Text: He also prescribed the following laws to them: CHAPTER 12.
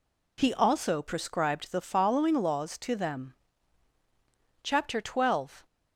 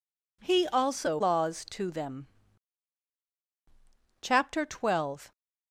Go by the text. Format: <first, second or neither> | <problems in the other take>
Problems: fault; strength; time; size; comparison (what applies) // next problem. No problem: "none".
first | skips "prescribed the following"; at 1.1 s